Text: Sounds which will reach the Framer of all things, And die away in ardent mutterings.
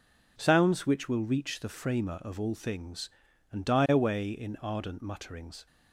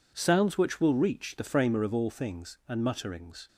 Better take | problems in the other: first | skips "die away in ardent"; at 2.8 s

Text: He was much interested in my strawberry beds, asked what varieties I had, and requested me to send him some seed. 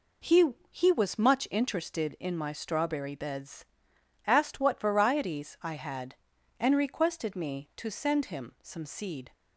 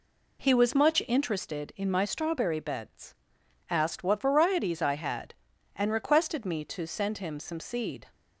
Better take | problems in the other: second | says "He" twice; at 0.7 s

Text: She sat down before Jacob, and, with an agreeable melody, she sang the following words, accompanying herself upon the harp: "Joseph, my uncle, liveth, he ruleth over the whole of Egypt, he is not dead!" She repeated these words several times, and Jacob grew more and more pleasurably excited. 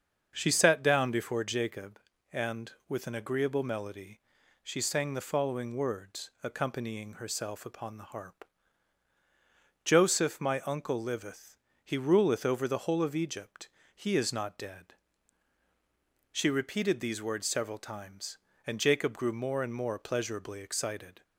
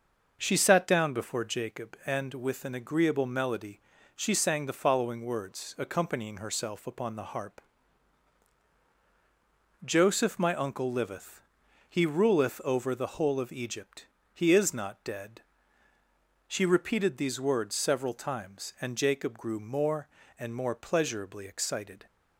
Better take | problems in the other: neither | starts louder than the rest; the same in both

